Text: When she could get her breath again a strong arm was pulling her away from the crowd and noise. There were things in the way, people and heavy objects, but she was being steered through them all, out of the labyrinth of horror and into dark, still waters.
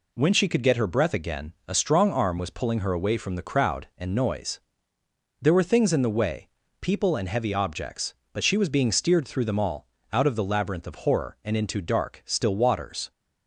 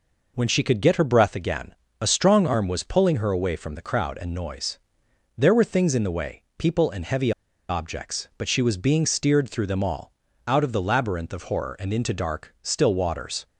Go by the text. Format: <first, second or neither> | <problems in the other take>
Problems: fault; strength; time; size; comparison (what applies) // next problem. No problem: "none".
first | pauses between "again" and "a"; slight; at 1.7 s; 0.26 s long // pauses between "heavy" and "objects"; at 7.3 s; 0.38 s long